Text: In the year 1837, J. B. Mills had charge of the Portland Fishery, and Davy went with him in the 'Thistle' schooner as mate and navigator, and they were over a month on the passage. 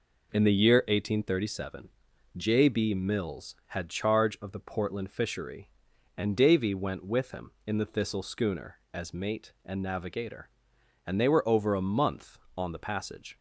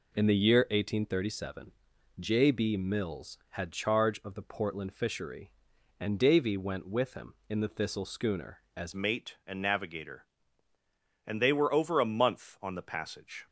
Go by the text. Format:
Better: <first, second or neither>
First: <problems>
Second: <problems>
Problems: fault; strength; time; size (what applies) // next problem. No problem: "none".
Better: first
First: none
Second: changes voice at "mate"; from 8.9 s on; 4.5 s long